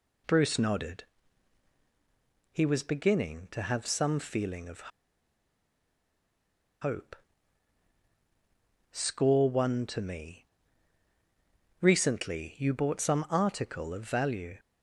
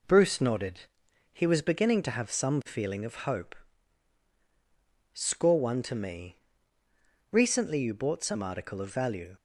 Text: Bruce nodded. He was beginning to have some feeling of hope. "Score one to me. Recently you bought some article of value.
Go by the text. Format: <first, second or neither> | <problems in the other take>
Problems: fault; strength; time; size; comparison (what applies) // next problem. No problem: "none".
second | pauses between "of" and "hope"; strong; at 4.8 s; 1.9 s long